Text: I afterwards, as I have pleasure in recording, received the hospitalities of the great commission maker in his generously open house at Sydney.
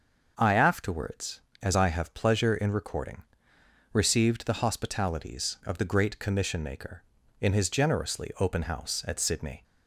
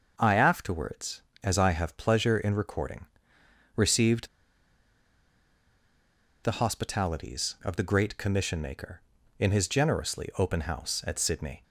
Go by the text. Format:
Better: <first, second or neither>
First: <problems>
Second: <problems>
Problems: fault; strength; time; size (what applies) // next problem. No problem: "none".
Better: first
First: starts louder than the rest; noticeable; until 1.3 s; 6 dB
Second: starts louder than the rest; noticeable; until 1.1 s; 6 dB // pauses between "received" and "the"; strong; at 4.2 s; 2.1 s long